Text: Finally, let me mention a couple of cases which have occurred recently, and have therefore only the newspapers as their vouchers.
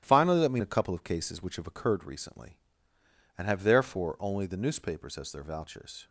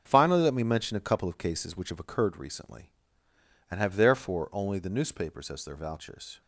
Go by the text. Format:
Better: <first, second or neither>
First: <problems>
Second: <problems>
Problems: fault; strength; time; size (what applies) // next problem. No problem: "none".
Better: second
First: starts louder than the rest; strong; until 1.0 s; 12.5 dB // skips "mention"; at 0.6 s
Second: starts louder than the rest; until 1.0 s; 7 dB